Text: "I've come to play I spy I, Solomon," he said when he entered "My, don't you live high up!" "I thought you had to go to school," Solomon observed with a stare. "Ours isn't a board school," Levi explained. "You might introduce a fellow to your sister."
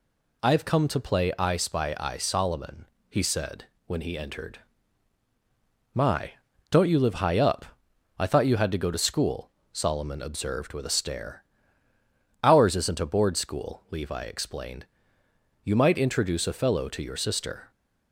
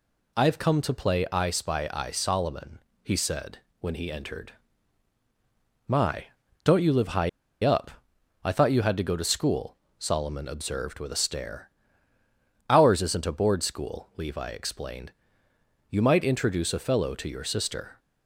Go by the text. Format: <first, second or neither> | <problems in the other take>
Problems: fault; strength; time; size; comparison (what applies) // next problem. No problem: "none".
first | pauses between "said" and "when"; slight; at 3.5 s; 0.22 s long; slight in the first // pauses between "entered" and "My"; strong; at 4.5 s; 1.3 s long; strong in the first // pauses between "high" and "up"; slight; at 7.2 s; 0.33 s long